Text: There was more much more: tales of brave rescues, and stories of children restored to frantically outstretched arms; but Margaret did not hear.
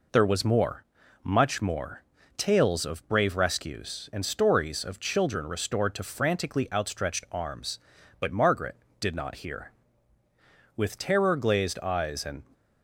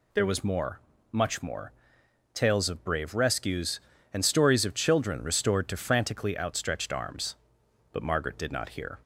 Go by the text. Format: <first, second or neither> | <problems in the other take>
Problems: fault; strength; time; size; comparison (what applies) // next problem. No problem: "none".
second | pauses between "more" and "much"; at 0.8 s; 0.40 s long; slight in the second // goes on to say "With terror glazed eyes and"; strong; from 10.7 s on; 1.6 s long